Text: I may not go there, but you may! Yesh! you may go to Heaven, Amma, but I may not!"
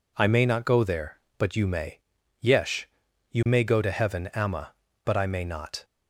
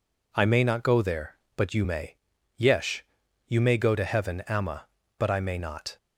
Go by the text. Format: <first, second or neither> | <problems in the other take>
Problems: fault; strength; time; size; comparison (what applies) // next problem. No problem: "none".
neither | none